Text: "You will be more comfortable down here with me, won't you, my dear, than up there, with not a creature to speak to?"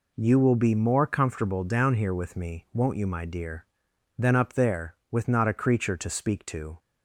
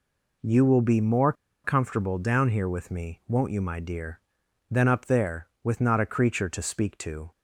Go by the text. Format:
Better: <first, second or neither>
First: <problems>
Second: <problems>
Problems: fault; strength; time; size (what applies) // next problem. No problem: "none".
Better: first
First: none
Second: pauses between "more" and "comfortable"; slight; at 1.3 s; 0.31 s long